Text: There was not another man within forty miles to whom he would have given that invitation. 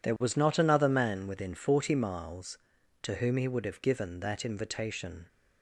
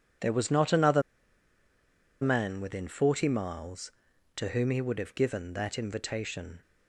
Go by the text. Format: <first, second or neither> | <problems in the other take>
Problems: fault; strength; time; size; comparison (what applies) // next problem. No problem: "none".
first | pauses between "another" and "man"; at 1.0 s; 1.1 s long